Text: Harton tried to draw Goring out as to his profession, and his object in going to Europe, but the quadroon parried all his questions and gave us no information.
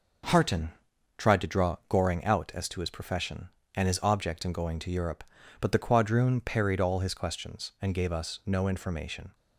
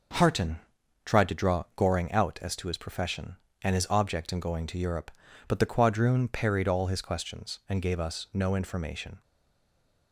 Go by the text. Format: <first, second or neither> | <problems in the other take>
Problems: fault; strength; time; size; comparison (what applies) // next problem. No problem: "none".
first | pauses between "Harton" and "tried"; noticeable; at 0.5 s; 0.48 s long; noticeable in the first // stays silent after the last word; slight; from 9.2 s on; 0.9 s long